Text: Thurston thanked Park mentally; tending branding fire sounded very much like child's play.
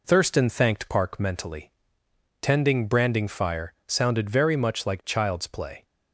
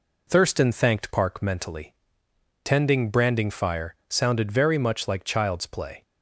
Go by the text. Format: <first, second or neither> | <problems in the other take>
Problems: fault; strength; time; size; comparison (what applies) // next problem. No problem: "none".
neither | none